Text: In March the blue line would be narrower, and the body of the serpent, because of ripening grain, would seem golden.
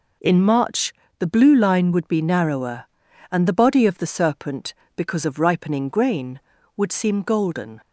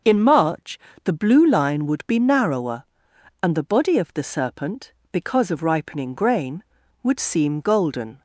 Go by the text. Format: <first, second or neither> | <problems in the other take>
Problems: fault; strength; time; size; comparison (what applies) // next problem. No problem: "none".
neither | pauses between "March" and "the"; slight; the same in both